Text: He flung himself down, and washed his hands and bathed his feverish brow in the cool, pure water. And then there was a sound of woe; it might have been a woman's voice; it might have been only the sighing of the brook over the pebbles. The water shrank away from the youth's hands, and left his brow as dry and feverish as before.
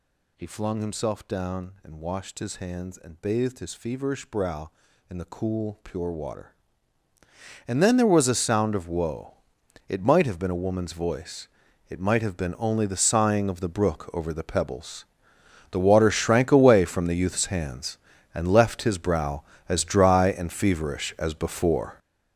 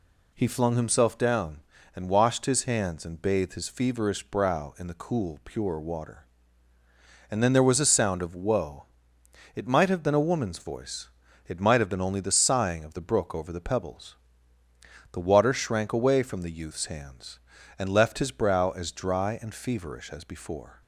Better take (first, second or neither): second